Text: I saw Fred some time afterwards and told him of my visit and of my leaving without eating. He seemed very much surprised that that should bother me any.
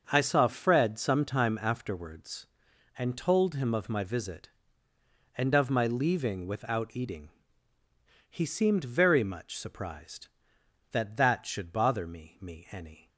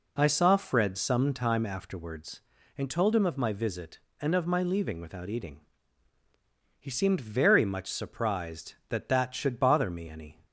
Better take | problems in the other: second | starts louder than the rest; until 1.1 s; 6.5 dB // says "me" twice; at 12.4 s

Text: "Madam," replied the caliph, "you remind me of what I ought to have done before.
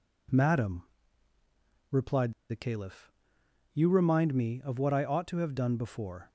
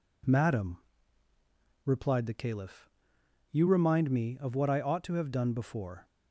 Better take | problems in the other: second | pauses between "replied" and "the"; slight; at 2.3 s; 0.18 s long

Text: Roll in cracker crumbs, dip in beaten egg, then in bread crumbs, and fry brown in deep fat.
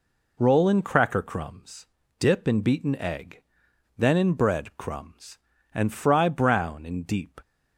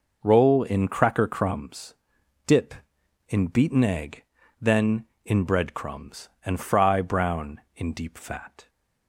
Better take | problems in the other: second | stops before "fat"; at 7.4 s

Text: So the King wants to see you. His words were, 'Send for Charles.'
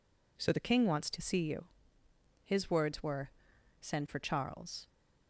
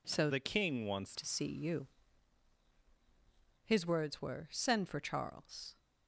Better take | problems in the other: first | changes voice from "the" to "wants"; from 0.3 to 1.1 s; 0.8 s long

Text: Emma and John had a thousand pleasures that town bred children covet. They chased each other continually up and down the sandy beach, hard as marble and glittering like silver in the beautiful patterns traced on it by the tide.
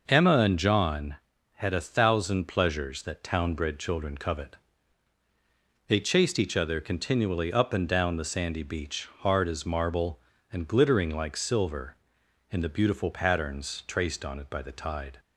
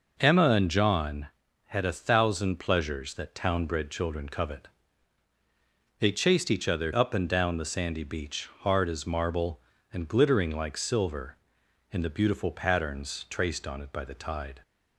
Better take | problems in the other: first | skips "continually"; at 6.9 s

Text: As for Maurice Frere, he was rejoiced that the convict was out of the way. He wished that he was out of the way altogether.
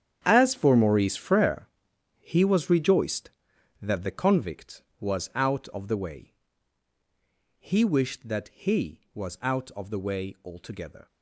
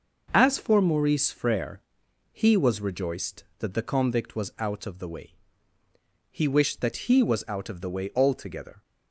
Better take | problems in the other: second | gets quieter; strong; throughout; 14 dB

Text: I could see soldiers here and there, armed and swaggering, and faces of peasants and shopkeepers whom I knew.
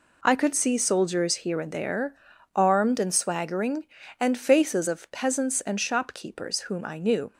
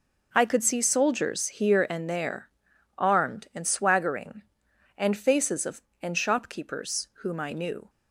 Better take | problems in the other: first | skips "peasants"; at 5.9 s

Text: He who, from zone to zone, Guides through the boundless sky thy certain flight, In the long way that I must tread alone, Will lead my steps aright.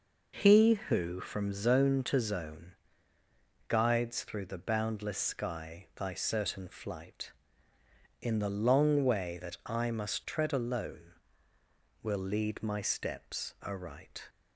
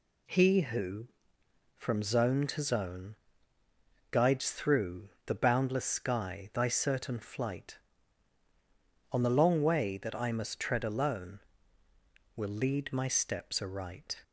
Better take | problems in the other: first | pauses between "through" and "the"; slight; at 5.0 s; 0.16 s long // says "On" for "In"; at 9.1 s

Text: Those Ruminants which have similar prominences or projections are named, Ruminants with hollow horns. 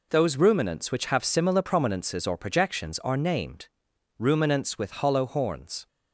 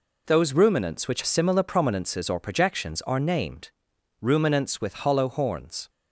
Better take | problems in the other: first | skips "have"; at 1.2 s

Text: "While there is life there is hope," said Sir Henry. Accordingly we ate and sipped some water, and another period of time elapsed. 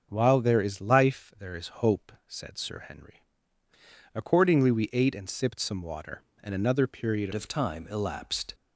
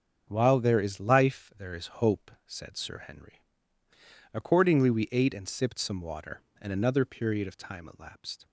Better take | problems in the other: second | starts louder than the rest; until 1.1 s; 6.5 dB; also in the second // changes voice at "of"; from 7.3 s on; 1.2 s long

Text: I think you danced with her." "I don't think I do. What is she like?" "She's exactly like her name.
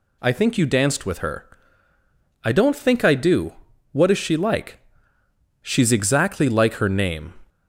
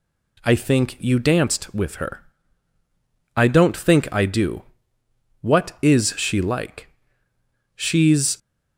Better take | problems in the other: first | stops before "exactly like her name"; at 8.3 s

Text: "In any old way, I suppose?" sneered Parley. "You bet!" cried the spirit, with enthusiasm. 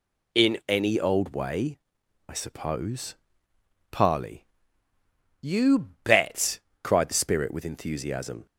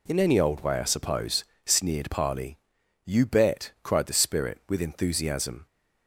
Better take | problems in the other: second | skips "sneered"; at 3.5 s // pauses between "You" and "bet"; slight; at 5.8 s; 0.16 s long

